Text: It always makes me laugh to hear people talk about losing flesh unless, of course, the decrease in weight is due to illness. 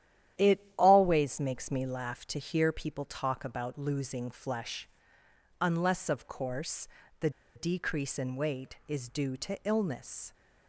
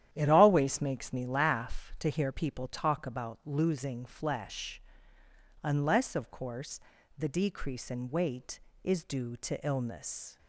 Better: second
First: starts louder than the rest; strong; until 1.5 s; 11 dB // pauses between "flesh" and "unless"; noticeable; at 4.8 s; 0.76 s long // pauses between "the" and "decrease"; slight; at 7.2 s; 0.25 s long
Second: starts louder than the rest; strong; until 1.1 s; 11 dB // pauses between "flesh" and "unless"; noticeable; at 4.8 s; 0.80 s long

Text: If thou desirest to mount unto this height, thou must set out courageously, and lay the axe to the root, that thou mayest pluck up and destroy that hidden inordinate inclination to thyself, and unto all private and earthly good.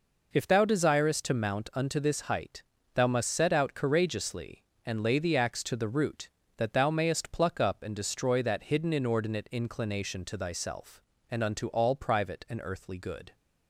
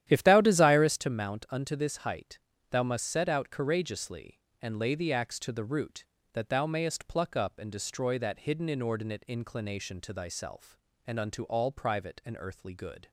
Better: first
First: none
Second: starts louder than the rest; strong; until 1.1 s; 11.5 dB

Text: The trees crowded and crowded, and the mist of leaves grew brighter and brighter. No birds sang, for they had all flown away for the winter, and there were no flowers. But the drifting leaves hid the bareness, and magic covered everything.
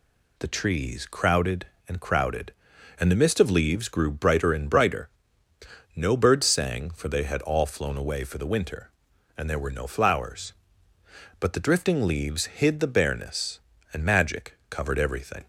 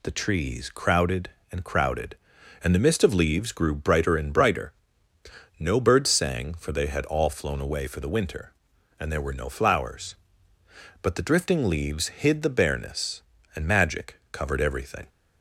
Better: neither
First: none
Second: none

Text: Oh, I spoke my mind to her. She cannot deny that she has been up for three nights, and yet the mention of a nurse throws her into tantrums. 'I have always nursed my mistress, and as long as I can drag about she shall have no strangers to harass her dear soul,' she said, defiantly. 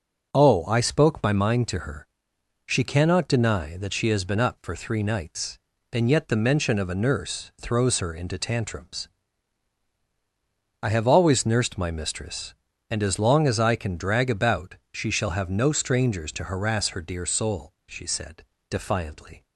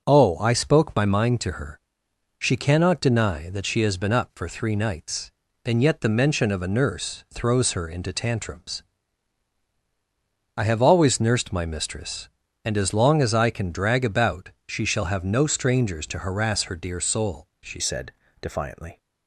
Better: first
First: pauses between "about" and "she"; slight; at 14.7 s; 0.16 s long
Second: starts louder than the rest; noticeable; until 1.0 s; 6 dB // pauses between "about" and "she"; slight; at 14.4 s; 0.16 s long // changes voice at "said"; from 17.7 s on; 1.2 s long

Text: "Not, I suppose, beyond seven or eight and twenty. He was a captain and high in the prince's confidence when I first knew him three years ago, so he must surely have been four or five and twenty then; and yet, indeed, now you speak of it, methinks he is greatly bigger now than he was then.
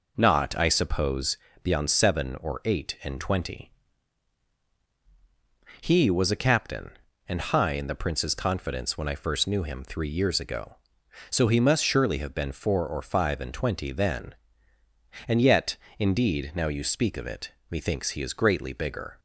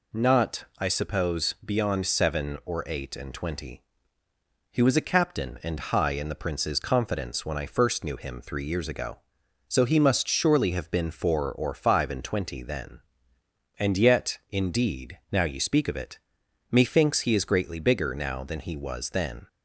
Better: second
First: stops before "now than he was then"; at 19.1 s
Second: none

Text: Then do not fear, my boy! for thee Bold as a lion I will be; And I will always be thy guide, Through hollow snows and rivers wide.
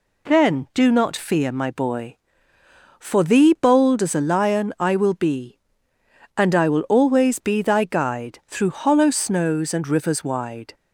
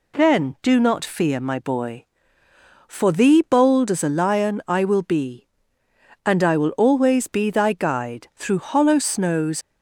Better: first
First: none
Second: stops before "and rivers wide"; at 9.6 s

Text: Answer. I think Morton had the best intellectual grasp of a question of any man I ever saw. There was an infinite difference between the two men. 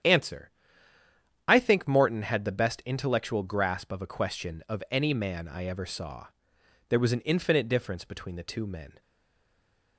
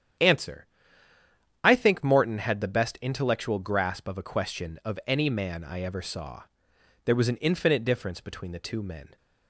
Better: second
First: starts louder than the rest; strong; until 2.0 s; 9.5 dB // stays silent after the last word; from 9.0 s on; 0.9 s long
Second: starts louder than the rest; strong; until 2.1 s; 9.5 dB

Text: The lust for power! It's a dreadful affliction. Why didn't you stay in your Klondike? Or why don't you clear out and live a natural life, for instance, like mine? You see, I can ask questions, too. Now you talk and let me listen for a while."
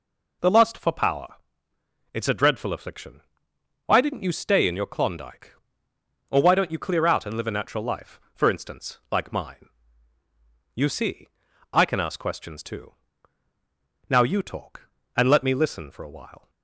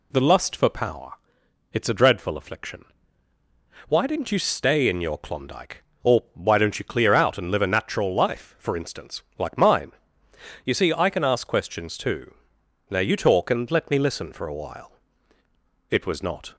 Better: first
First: none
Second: goes on to say "It was not"; noticeable; from 15.8 s on; 0.66 s long

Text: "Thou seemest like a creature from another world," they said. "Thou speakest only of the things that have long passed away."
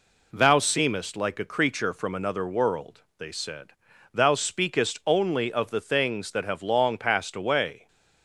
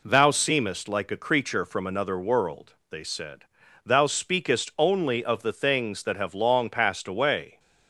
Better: neither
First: none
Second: none

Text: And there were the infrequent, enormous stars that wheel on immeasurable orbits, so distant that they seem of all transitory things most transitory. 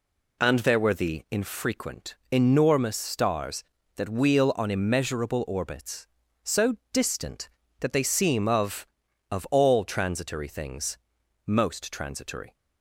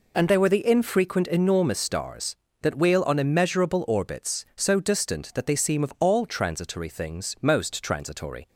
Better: second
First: pauses between "so" and "distant"; slight; at 6.7 s; 0.16 s long // says "of" twice; at 9.3 s // pauses between "things" and "most"; noticeable; at 10.9 s; 0.48 s long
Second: none

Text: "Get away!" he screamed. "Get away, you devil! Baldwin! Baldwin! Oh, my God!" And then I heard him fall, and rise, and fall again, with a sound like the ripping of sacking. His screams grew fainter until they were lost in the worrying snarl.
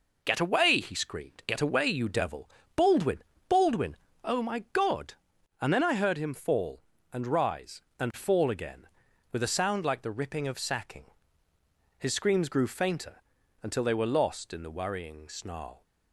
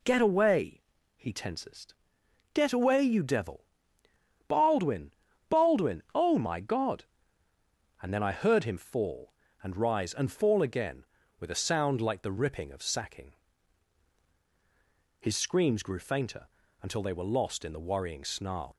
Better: first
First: pauses between "fainter" and "until"; at 13.2 s; 0.40 s long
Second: says "tensest" for "screamed"; at 1.3 s // pauses between "fainter" and "until"; slight; at 16.4 s; 0.34 s long

